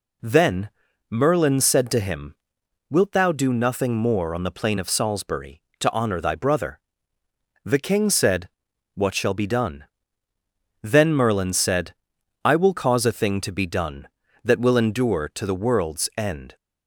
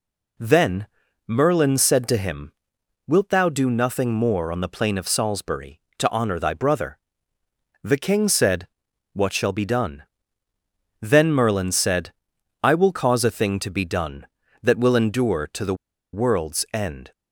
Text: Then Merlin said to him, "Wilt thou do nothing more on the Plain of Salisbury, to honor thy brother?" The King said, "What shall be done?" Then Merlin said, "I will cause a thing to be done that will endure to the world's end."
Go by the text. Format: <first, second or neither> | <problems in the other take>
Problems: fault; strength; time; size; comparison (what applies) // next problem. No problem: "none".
first | pauses between "Then" and "Merlin"; at 0.8 s; 0.40 s long; also in the first // pauses between "the" and "world's"; at 15.7 s; 0.38 s long